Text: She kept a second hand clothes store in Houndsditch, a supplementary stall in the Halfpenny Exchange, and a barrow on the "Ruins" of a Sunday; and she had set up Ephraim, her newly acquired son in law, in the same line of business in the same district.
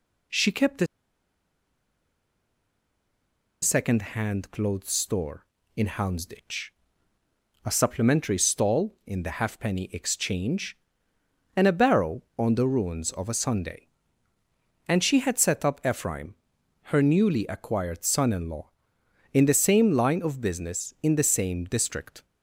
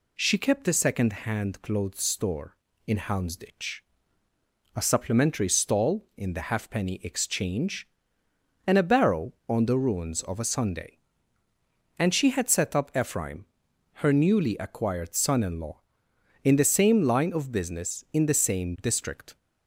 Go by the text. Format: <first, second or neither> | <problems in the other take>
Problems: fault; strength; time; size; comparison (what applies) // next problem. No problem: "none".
second | pauses between "a" and "second"; strong; at 0.8 s; 2.7 s long